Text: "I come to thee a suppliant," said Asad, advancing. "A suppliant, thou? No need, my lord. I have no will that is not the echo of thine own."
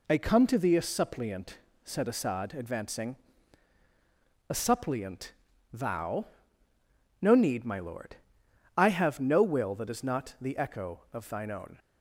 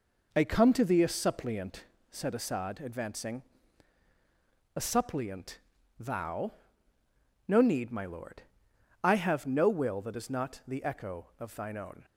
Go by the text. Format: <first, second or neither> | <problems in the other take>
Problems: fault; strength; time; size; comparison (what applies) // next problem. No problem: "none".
first | starts louder than the rest; noticeable; until 2.0 s; 4.5 dB